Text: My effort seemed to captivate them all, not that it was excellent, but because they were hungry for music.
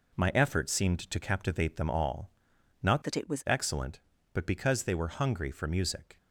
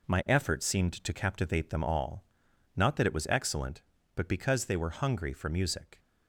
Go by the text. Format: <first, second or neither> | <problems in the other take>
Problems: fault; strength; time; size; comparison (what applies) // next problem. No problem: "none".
second | changes voice from "that" to "was"; from 3.0 to 3.4 s; 0.4 s long